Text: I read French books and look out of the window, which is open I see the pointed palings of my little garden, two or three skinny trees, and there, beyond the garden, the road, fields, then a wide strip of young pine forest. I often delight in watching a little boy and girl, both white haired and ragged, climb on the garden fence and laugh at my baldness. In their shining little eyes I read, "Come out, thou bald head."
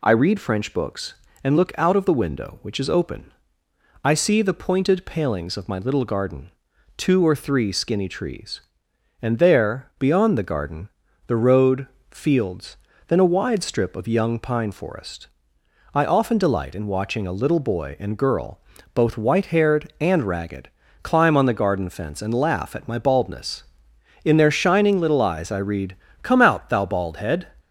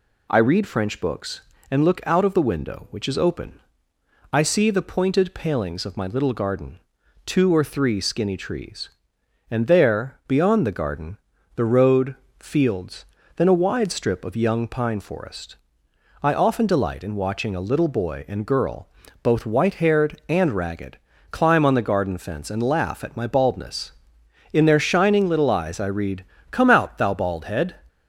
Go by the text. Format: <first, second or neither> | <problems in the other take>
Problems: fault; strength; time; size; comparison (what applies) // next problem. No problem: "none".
neither | pauses between "open" and "I"; noticeable; the same in both